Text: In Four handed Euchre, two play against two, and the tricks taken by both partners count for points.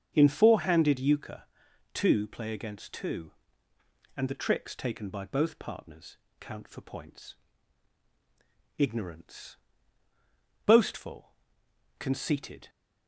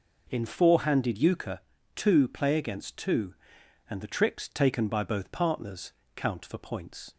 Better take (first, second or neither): second